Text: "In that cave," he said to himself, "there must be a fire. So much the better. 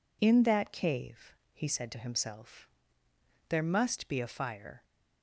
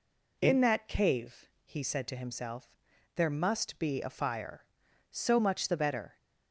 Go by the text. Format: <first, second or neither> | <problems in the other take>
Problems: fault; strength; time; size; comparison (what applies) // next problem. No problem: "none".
second | stops before "So much the better"; at 4.8 s